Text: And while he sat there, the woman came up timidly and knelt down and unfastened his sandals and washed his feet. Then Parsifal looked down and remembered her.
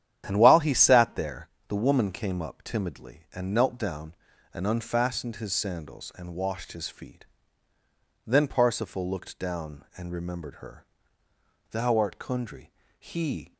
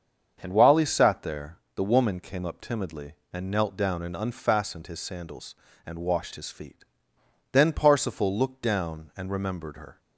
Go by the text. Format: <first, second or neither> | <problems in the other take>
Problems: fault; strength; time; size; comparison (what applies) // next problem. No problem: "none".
second | starts louder than the rest; strong; until 1.2 s; 10 dB; also in the second // goes on to say "Thou art Kundry he"; strong; from 11.7 s on; 1.8 s long